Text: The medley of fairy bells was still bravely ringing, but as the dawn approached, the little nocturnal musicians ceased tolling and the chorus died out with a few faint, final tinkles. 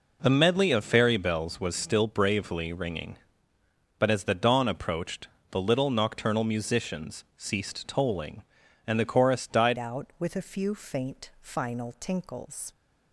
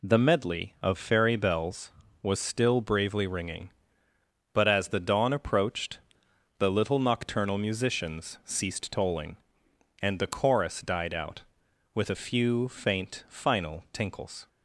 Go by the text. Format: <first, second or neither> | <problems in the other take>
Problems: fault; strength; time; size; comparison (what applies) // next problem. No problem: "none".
second | changes voice at "out"; from 9.7 s on; 3.0 s long